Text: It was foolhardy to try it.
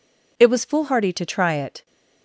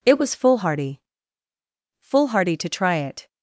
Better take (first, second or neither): first